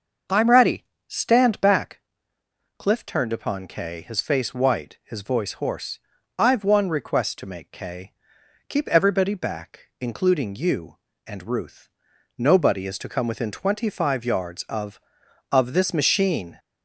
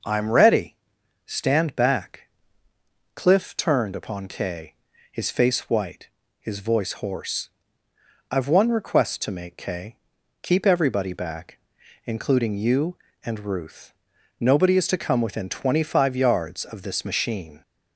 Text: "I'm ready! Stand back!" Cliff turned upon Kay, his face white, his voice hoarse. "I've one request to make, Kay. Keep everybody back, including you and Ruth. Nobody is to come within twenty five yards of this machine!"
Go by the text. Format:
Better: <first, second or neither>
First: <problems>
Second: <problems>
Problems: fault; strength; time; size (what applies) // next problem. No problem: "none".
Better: second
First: starts louder than the rest; noticeable; until 1.5 s; 6 dB // says "of" twice; at 15.5 s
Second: none